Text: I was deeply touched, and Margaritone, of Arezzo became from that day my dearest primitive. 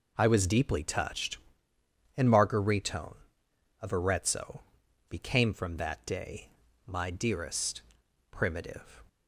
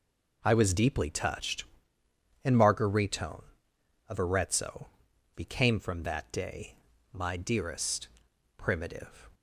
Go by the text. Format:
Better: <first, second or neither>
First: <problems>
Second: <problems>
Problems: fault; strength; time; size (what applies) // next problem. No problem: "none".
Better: neither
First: pauses between "Arezzo" and "became"; noticeable; at 4.6 s; 0.48 s long // pauses between "day" and "my"; at 6.4 s; 0.40 s long // pauses between "dearest" and "primitive"; noticeable; at 7.8 s; 0.50 s long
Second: pauses between "Arezzo" and "became"; noticeable; at 4.8 s; 0.48 s long // pauses between "day" and "my"; at 6.7 s; 0.40 s long // pauses between "dearest" and "primitive"; noticeable; at 8.0 s; 0.50 s long